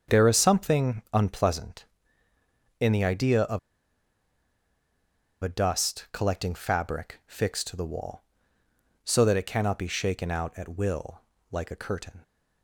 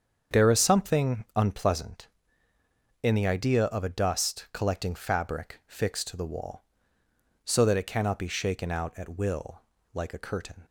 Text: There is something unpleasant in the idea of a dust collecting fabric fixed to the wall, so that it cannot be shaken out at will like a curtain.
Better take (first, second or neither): second